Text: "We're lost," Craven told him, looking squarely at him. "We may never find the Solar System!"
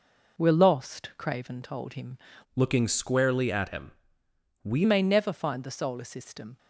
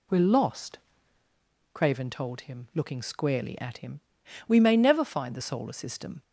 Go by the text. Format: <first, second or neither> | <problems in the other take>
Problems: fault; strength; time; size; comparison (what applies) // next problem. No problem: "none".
second | changes voice from "looking" to "We"; from 2.5 to 4.8 s; 2.3 s long